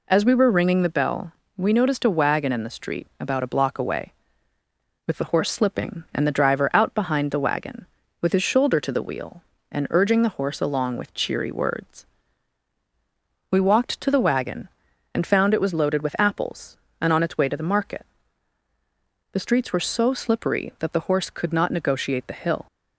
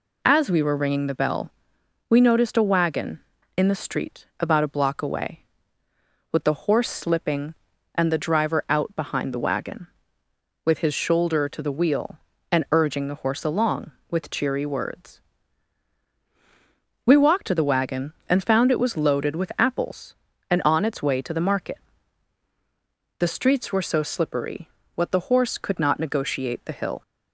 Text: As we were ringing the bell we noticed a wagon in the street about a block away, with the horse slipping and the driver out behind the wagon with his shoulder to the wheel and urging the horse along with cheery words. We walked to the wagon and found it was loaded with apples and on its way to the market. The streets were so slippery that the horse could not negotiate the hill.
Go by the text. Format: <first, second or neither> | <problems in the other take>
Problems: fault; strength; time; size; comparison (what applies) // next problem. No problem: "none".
first | pauses between "bell" and "we"; noticeable; at 1.4 s; 0.58 s long; slight in the first // says "what" for "that"; at 24.9 s